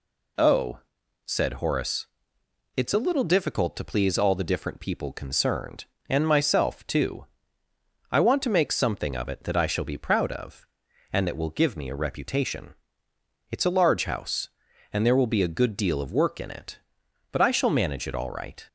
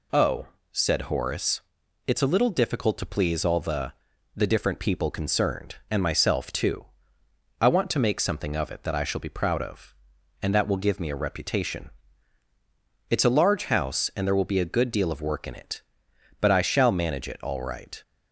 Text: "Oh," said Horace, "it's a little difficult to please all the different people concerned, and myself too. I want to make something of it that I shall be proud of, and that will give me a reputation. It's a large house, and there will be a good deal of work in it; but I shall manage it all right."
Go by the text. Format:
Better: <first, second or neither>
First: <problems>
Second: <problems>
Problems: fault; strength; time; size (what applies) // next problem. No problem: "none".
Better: first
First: none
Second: says "the" twice; at 4.3 s